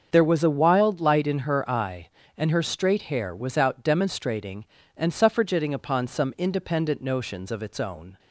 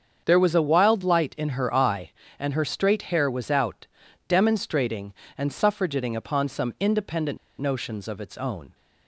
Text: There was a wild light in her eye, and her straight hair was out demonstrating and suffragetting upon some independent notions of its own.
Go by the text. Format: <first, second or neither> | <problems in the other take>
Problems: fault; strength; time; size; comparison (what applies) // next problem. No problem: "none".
first | starts louder than the rest; until 1.2 s; 7 dB; also in the first // pauses between "out" and "demonstrating"; at 3.8 s; 0.42 s long // pauses between "independent" and "notions"; slight; at 7.3 s; 0.21 s long